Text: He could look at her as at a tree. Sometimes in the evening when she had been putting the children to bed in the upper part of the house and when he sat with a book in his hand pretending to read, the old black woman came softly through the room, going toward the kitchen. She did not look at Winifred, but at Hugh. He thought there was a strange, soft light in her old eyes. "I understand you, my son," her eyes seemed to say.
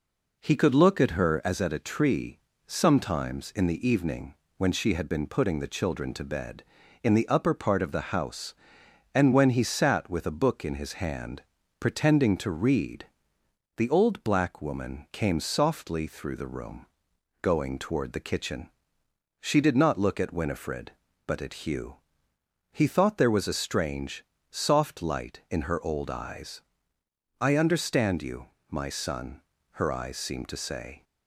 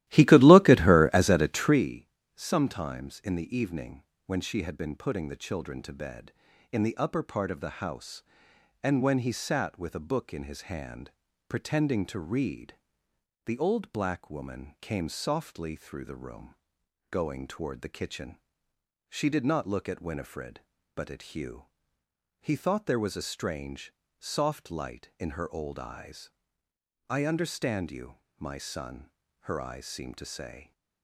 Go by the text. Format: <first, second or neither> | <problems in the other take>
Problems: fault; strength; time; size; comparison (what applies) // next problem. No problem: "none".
first | starts louder than the rest; strong; until 2.0 s; 15 dB // pauses between "evening" and "when"; slight; at 4.0 s; 0.22 s long; slight in the first // pauses between "hand" and "pretending"; at 11.1 s; 0.38 s long; also in the first